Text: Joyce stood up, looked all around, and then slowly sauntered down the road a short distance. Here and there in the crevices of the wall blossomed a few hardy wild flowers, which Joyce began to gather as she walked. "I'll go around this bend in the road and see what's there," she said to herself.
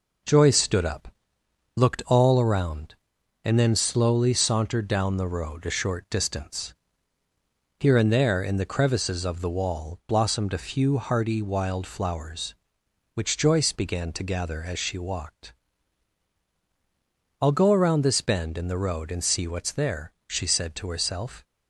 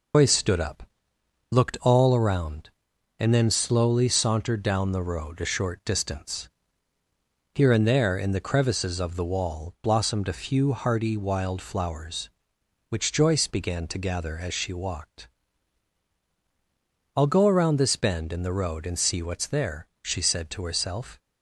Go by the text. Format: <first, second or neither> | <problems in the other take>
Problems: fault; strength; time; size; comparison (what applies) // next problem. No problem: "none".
first | loses the start of "Joyce"; at 0.1 s; 145 ms